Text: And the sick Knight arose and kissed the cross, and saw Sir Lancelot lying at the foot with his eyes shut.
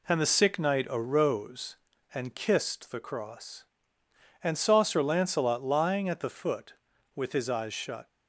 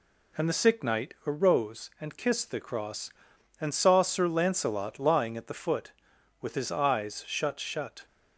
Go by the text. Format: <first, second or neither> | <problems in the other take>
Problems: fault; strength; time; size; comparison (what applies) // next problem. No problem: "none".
first | says "shut" twice; at 7.5 s